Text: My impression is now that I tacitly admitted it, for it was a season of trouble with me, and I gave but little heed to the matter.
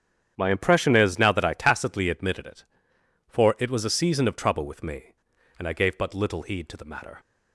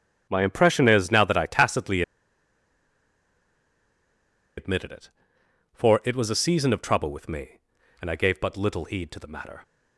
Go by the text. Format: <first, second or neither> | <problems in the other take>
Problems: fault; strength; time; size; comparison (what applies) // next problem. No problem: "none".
first | starts louder than the rest; strong; until 1.3 s; 9 dB; strong in the first // pauses between "tacitly" and "admitted"; strong; at 2.0 s; 2.5 s long